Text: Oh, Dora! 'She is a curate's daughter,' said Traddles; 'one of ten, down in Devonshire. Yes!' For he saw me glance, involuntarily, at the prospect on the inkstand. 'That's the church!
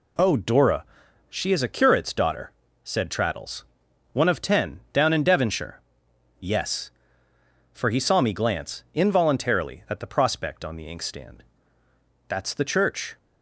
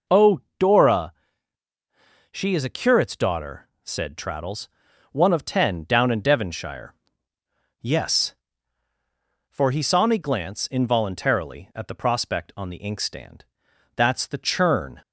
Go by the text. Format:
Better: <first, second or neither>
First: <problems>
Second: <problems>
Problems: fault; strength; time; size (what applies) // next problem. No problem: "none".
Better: first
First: none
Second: says "churn" for "church"; at 14.3 s